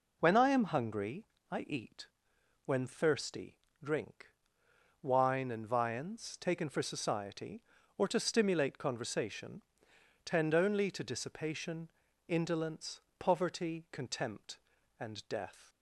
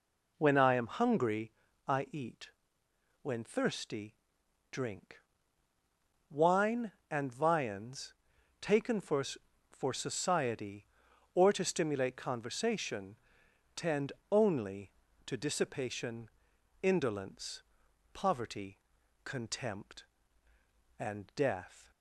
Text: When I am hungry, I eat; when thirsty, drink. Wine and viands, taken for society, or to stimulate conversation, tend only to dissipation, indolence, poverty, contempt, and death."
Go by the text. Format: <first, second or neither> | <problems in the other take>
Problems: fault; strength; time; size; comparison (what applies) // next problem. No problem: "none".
first | says "for" twice; at 9.7 s // pauses between "tend" and "only"; slight; at 14.1 s; 0.20 s long